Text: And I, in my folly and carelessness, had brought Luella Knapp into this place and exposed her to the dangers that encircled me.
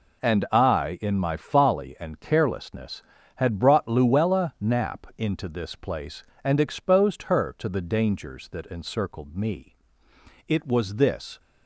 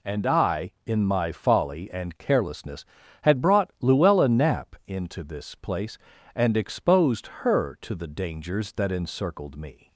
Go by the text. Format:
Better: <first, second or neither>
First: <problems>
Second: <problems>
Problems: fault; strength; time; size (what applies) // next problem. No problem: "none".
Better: second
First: goes on to say "It was this"; noticeable; from 10.4 s on; 0.92 s long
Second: none